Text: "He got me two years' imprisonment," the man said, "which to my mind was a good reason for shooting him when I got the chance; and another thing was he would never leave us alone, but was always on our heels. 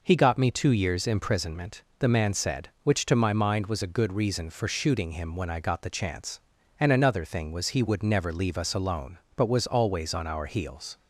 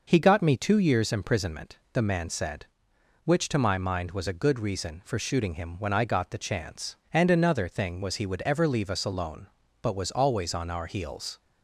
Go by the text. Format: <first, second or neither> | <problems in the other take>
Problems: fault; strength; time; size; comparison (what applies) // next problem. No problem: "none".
first | says "ever" for "never"; at 8.4 s